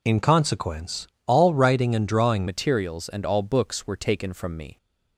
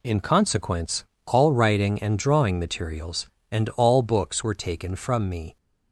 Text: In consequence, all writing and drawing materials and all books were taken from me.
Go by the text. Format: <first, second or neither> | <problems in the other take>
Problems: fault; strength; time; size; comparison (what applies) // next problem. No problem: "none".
second | changes voice at "materials"; from 2.4 s on; 2.3 s long